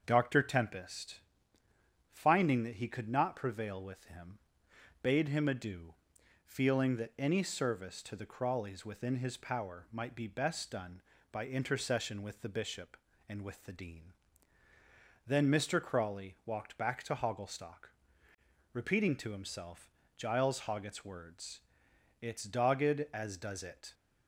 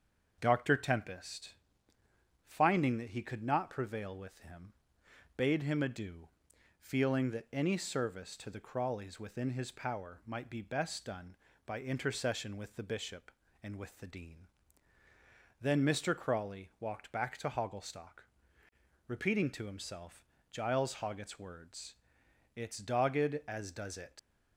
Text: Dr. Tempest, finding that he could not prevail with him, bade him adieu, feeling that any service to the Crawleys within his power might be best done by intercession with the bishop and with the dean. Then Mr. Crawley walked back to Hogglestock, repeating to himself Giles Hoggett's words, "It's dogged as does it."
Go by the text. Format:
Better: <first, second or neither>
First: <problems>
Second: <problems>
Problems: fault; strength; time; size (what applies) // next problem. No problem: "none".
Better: first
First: starts louder than the rest; until 1.0 s; 7 dB // pauses between "himself" and "Giles"; slight; at 19.8 s; 0.28 s long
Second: starts louder than the rest; until 1.4 s; 7 dB // pauses between "himself" and "Giles"; slight; at 20.2 s; 0.28 s long // leaves "it" unfinished; at 24.1 s; 85 ms